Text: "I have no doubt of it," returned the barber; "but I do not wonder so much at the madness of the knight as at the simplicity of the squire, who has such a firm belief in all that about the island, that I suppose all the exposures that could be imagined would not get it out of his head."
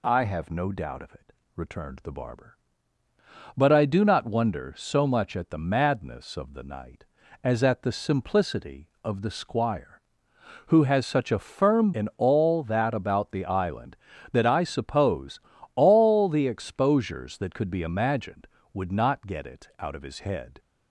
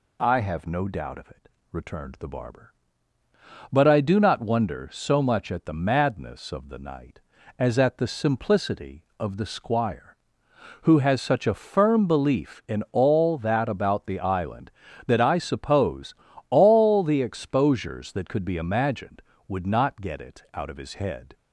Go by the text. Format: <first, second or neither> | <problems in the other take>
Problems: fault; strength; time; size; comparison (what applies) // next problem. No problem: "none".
second | skips "belief"; at 11.9 s // pauses between "suppose" and "all"; slight; at 15.3 s; 0.36 s long; slight in the second